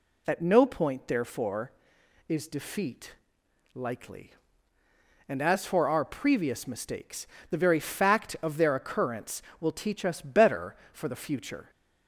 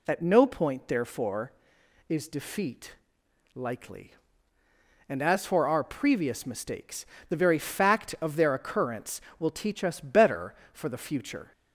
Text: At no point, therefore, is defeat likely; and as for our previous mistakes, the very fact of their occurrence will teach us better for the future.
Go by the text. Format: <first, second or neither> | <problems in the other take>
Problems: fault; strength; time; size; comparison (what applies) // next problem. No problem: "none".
neither | pauses between "defeat" and "likely"; noticeable; the same in both